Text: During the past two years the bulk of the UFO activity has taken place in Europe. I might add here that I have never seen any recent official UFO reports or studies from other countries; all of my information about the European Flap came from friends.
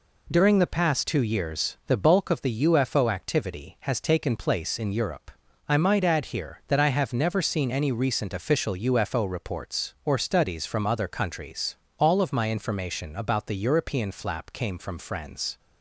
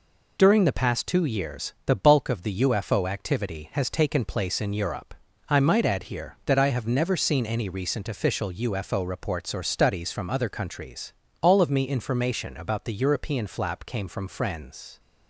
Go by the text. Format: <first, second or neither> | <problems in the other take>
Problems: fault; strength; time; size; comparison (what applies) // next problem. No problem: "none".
first | says "me" for "my"; at 11.6 s